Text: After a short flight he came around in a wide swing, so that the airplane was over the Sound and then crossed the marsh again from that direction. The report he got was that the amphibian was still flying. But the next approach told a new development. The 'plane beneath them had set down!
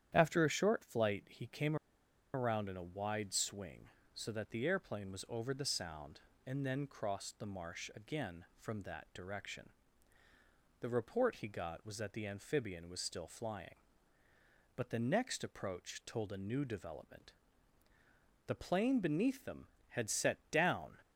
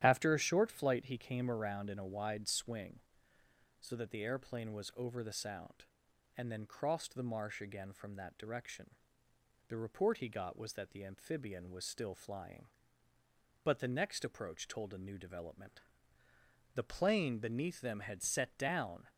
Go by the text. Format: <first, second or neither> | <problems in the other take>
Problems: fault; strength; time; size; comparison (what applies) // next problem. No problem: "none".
second | starts louder than the rest; strong; until 1.1 s; 10 dB; strong in the second // pauses between "came" and "around"; noticeable; at 1.7 s; 0.58 s long